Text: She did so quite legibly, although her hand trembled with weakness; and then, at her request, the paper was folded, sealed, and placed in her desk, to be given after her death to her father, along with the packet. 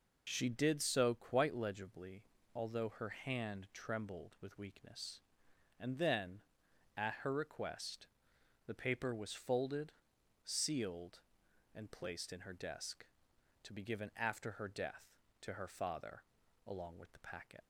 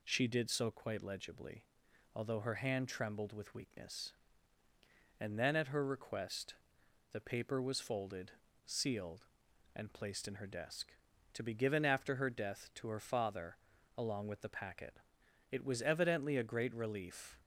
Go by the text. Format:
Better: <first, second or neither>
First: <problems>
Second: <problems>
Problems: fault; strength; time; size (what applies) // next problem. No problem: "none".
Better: first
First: none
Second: goes on to say "It was evidently a great relief"; strong; from 15.5 s on; 1.8 s long